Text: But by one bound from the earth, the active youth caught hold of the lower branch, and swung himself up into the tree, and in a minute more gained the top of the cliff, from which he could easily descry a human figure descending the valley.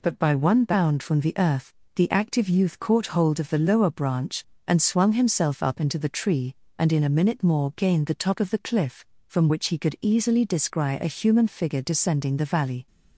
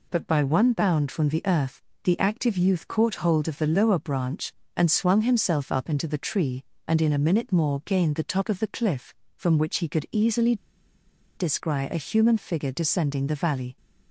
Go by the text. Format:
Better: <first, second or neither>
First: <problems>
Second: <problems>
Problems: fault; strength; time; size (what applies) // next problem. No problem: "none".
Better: first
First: none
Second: pauses between "easily" and "descry"; noticeable; at 10.5 s; 0.82 s long